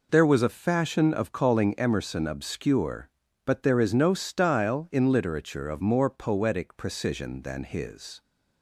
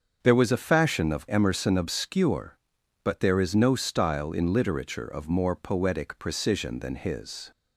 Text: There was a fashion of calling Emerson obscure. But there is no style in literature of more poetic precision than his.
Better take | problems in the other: first | starts louder than the rest; until 1.2 s; 7 dB // skips "calling"; at 1.2 s

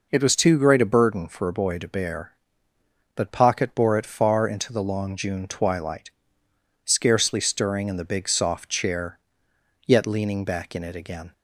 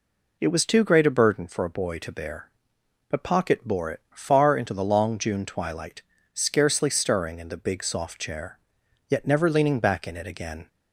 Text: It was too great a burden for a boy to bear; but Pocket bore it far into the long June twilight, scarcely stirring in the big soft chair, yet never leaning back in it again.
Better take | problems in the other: second | skips "never"; at 10.0 s

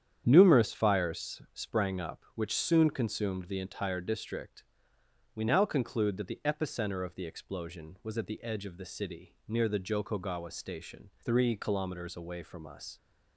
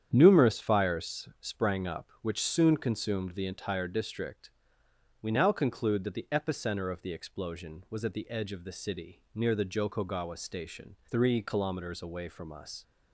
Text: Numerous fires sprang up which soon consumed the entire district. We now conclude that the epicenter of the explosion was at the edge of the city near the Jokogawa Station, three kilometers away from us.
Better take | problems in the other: neither | starts louder than the rest; strong; the same in both

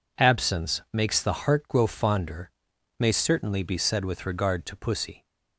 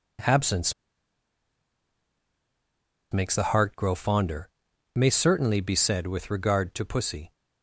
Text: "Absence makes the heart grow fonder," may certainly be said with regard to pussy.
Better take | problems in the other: first | pauses between "Absence" and "makes"; strong; at 0.7 s; 2.4 s long

